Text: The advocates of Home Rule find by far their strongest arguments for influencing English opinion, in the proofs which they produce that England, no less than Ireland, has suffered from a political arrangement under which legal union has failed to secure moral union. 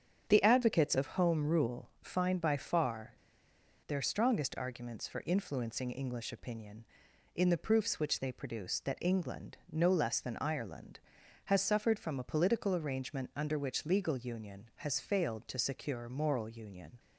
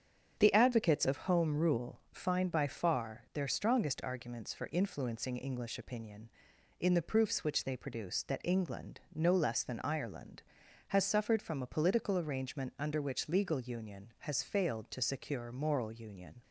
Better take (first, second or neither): second